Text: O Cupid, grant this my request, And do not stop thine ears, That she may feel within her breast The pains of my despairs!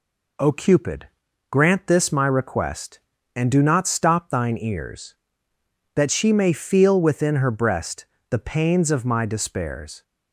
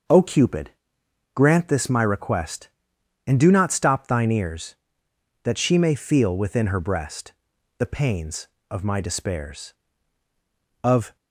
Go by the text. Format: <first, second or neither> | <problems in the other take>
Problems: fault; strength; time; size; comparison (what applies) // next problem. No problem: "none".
first | starts louder than the rest; until 1.7 s; 6.5 dB // pauses between "breast" and "The"; noticeable; at 7.3 s; 0.46 s long; slight in the first // goes on to say "Of"; slight; from 10.8 s on; 0.32 s long